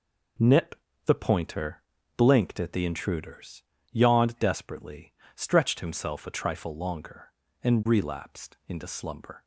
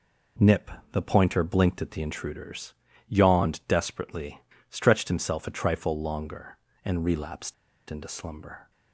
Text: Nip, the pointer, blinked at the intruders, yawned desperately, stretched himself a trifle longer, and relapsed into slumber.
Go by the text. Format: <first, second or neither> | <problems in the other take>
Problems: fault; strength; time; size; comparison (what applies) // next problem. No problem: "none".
first | pauses between "relapsed" and "into"; at 7.5 s; 0.36 s long